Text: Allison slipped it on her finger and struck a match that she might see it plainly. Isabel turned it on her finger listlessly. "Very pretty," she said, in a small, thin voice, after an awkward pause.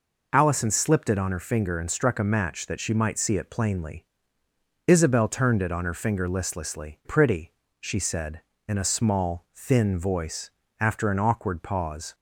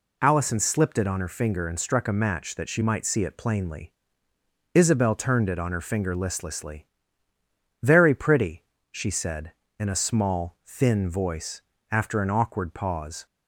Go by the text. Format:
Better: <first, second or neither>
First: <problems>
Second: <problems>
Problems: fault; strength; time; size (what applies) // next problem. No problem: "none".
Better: second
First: skips "Very"; at 7.0 s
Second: none